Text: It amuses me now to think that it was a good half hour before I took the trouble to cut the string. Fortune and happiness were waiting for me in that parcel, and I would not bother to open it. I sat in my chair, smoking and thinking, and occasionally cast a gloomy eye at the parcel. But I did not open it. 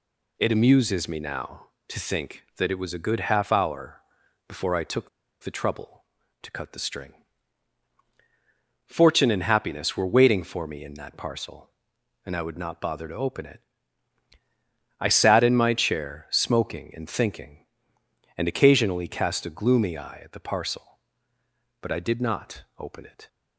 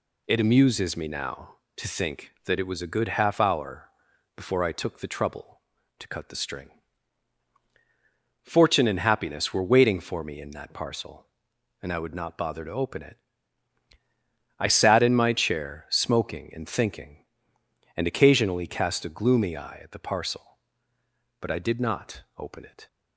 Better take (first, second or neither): second